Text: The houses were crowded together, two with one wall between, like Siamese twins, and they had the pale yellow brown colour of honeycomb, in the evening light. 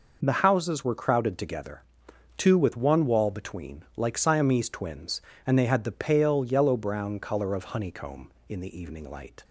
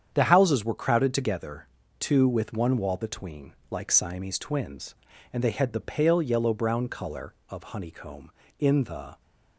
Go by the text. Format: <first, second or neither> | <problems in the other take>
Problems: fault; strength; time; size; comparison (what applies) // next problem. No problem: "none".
first | starts louder than the rest; strong; until 1.1 s; 8 dB // stops before "evening light"; at 9.2 s